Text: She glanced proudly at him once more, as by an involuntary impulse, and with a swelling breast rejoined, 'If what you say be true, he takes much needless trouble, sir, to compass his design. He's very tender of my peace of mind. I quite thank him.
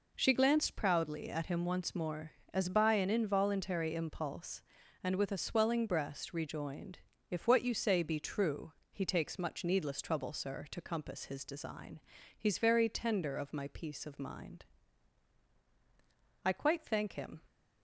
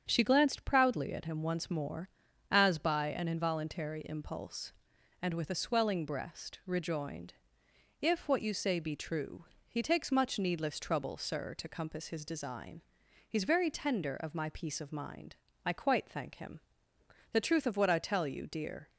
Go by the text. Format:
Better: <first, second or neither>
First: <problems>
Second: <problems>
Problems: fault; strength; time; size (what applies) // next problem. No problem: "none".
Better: first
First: none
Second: starts louder than the rest; strong; until 1.1 s; 7.5 dB // goes on to say "The truth of what I tell you dear"; from 17.3 s on; 1.5 s long